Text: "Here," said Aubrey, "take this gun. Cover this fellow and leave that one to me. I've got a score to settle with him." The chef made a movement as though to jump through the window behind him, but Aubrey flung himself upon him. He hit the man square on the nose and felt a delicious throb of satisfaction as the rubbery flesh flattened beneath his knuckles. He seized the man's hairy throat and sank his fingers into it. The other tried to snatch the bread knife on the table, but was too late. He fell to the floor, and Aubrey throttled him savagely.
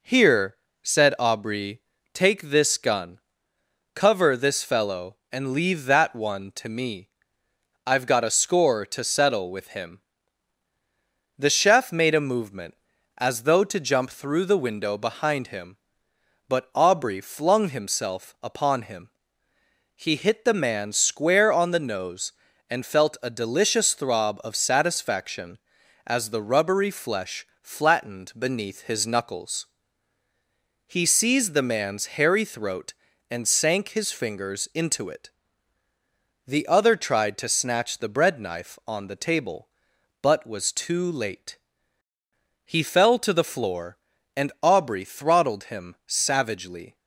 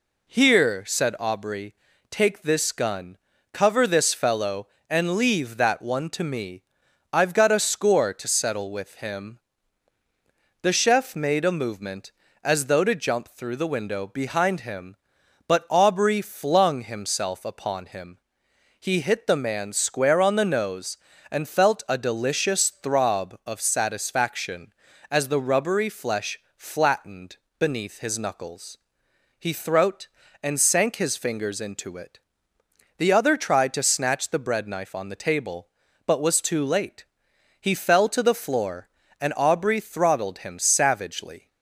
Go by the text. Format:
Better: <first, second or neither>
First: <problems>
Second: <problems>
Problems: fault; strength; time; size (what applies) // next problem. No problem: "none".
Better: first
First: pauses between "flesh" and "flattened"; slight; at 27.4 s; 0.16 s long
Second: pauses between "flesh" and "flattened"; slight; at 26.3 s; 0.16 s long // pauses between "flattened" and "beneath"; slight; at 27.3 s; 0.20 s long // skips "seized the man's hairy"; at 29.5 s